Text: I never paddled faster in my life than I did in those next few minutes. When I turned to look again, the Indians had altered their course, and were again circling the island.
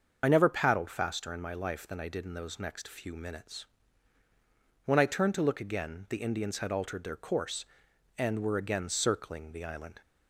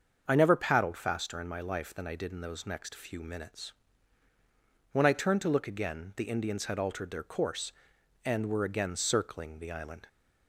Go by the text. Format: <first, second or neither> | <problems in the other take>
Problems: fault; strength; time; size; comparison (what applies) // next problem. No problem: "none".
second | loses the start of "I"; at 0.2 s; 25 ms // starts louder than the rest; until 1.2 s; 6.5 dB; also in the second